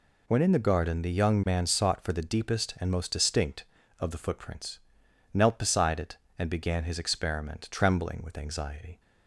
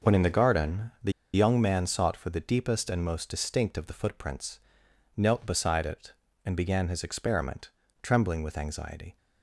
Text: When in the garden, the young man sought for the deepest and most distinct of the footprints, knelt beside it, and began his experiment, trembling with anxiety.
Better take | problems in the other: first | pauses between "the" and "young"; slight; at 1.1 s; 0.22 s long

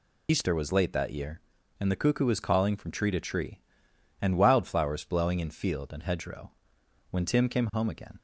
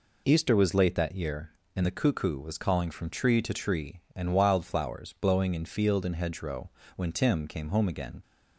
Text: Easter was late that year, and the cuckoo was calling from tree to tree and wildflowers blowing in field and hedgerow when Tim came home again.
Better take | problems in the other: second | loses the start of "Easter"; at 0.2 s; 80 ms // pauses between "hedgerow" and "when"; noticeable; at 6.5 s; 0.60 s long; slight in the second

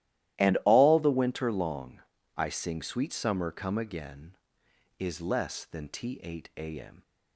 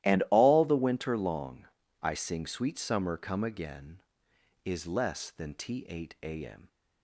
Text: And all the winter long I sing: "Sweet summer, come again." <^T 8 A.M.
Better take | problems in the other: neither | starts louder than the rest; strong; the same in both // pauses between "long" and "I"; slight; the same in both

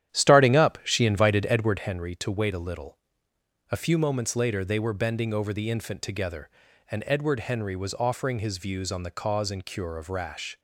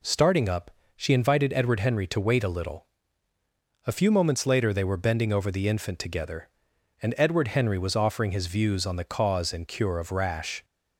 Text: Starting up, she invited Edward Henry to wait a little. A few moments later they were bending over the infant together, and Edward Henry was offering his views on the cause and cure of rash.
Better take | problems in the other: second | starts louder than the rest; strong; until 1.9 s; 10.5 dB

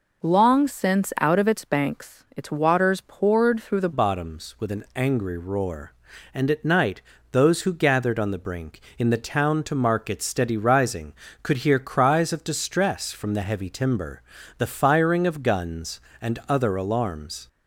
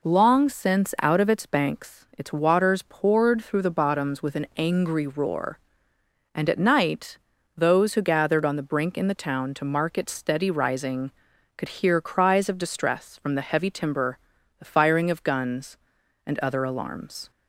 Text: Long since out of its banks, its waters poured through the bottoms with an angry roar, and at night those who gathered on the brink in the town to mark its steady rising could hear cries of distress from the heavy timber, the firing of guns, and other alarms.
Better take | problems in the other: second | changes voice at "bottoms"; from 3.9 s on; 13.5 s long // pauses between "night" and "those"; slight; at 7.0 s; 0.30 s long; also in the second

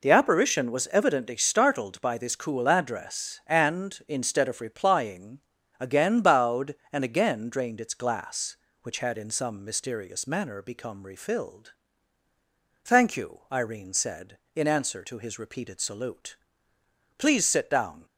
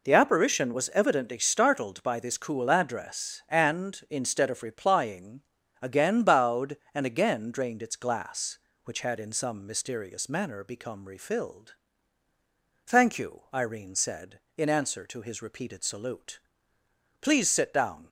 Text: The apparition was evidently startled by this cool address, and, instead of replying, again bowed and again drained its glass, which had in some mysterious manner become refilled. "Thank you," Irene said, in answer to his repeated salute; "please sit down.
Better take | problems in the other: neither | none

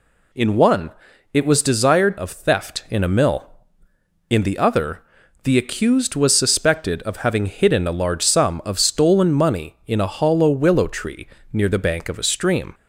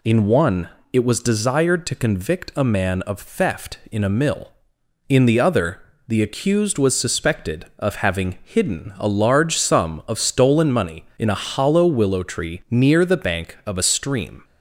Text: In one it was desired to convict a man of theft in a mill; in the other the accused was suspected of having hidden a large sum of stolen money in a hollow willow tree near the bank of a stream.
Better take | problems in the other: second | pauses between "one" and "it"; at 0.8 s; 0.44 s long; slight in the second // skips "to convict a man"; at 2.1 s // pauses between "other" and "the"; at 4.9 s; 0.44 s long; slight in the second // pauses between "tree" and "near"; slight; at 11.2 s; 0.28 s long

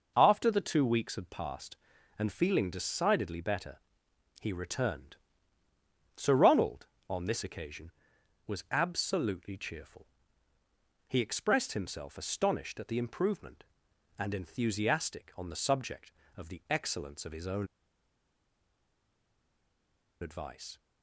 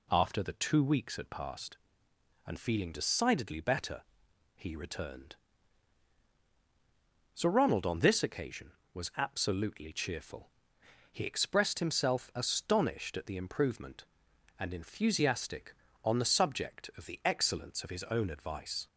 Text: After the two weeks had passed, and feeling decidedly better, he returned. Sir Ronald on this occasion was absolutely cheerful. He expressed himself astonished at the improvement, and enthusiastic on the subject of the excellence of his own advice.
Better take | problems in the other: second | pauses between "own" and "advice"; strong; at 17.6 s; 2.5 s long

